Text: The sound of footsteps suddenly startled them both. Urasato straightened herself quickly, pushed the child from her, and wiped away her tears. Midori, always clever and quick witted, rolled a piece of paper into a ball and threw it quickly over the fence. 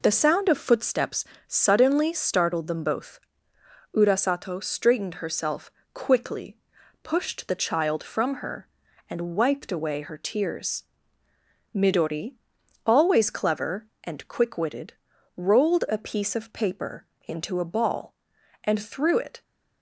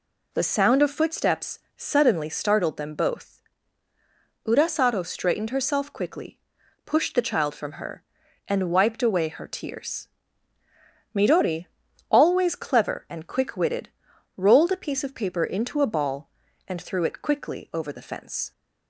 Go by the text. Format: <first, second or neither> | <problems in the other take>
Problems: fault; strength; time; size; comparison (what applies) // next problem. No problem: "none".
second | pauses between "footsteps" and "suddenly"; slight; at 1.2 s; 0.22 s long; slight in the second // pauses between "herself" and "quickly"; slight; at 5.6 s; 0.24 s long // pauses between "paper" and "into"; slight; at 17.0 s; 0.22 s long // stops before "quickly over the fence"; at 19.4 s